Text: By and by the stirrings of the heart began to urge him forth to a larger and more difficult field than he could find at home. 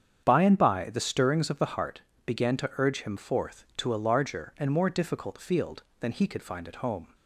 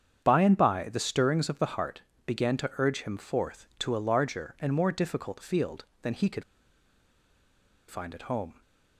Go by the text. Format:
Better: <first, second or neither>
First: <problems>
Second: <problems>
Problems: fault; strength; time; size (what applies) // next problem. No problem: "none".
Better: first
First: starts louder than the rest; strong; until 1.2 s; 8 dB // pauses between "heart" and "began"; slight; at 2.0 s; 0.24 s long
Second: starts louder than the rest; strong; until 1.2 s; 8 dB // pauses between "heart" and "began"; slight; at 2.0 s; 0.24 s long // pauses between "could" and "find"; strong; at 6.4 s; 1.4 s long